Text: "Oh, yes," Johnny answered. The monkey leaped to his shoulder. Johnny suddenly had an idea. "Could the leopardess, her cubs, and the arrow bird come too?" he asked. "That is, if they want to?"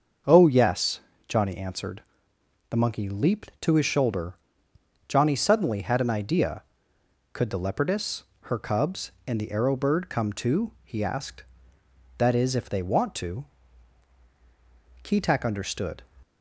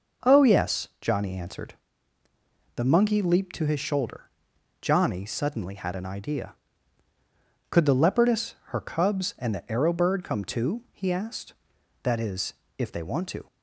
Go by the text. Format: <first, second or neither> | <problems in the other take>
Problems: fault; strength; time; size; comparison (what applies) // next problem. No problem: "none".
second | starts louder than the rest; until 1.5 s; 6.5 dB // goes on to say "Keetack understood"; noticeable; from 15.0 s on; 1.0 s long